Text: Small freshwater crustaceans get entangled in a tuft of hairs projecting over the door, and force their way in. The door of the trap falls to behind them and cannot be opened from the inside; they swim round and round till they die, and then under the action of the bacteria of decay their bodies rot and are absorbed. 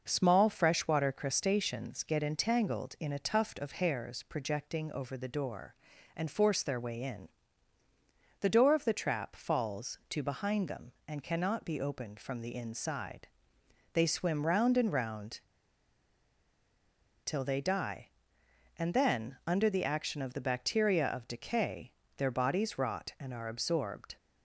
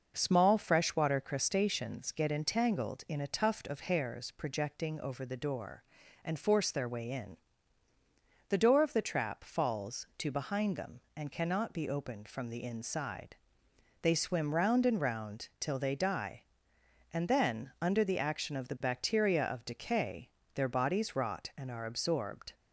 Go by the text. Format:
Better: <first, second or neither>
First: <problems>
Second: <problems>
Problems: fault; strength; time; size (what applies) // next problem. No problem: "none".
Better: second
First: pauses between "round" and "till"; strong; at 15.4 s; 1.8 s long // pauses between "decay" and "their"; slight; at 21.9 s; 0.26 s long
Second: pauses between "decay" and "their"; slight; at 20.2 s; 0.26 s long